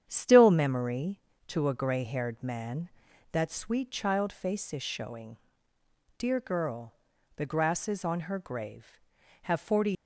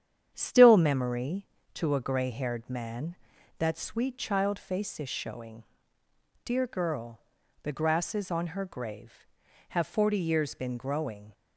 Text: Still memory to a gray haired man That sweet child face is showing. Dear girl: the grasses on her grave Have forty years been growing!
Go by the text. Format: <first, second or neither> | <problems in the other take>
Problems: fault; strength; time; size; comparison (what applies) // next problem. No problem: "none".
second | starts louder than the rest; strong; until 1.0 s; 9 dB; strong in the second // stops before "years been growing"; at 9.9 s